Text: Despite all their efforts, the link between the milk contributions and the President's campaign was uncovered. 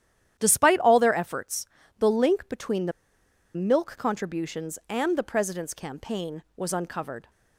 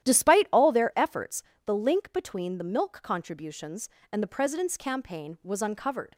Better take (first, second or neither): second